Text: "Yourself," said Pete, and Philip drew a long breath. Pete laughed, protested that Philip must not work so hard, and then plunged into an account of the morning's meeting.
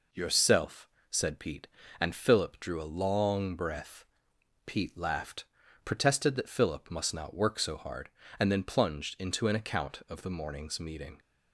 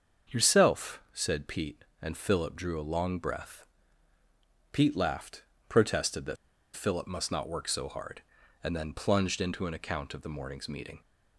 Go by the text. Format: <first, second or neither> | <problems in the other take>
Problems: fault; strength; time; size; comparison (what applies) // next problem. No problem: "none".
first | starts louder than the rest; until 1.4 s; 6.5 dB // pauses between "that" and "Philip"; at 6.3 s; 0.40 s long